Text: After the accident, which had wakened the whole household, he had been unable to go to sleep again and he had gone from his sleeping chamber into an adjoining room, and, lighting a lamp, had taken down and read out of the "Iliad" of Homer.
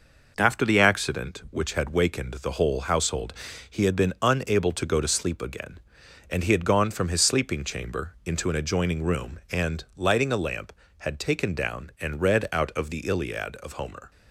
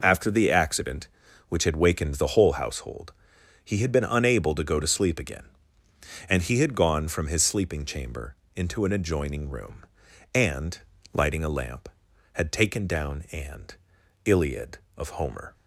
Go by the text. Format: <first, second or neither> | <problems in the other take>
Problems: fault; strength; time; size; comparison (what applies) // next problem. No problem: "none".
first | pauses between "chamber" and "into"; slight; at 8.3 s; 0.18 s long // skips "read out of the"; at 14.0 s